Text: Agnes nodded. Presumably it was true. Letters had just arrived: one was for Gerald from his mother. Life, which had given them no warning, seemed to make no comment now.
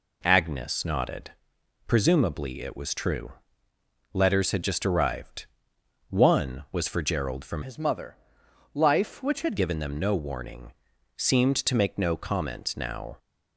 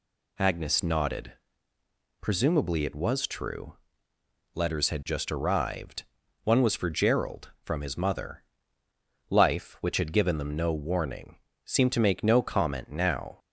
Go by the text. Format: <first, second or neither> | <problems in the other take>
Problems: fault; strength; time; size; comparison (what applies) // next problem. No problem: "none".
second | changes voice from "his" to "had"; from 7.6 to 9.5 s; 1.9 s long